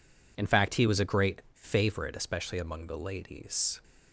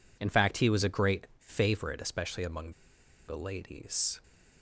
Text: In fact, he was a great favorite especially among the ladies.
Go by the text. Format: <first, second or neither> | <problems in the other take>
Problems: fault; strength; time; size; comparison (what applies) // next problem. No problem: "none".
first | pauses between "among" and "the"; noticeable; at 2.6 s; 0.58 s long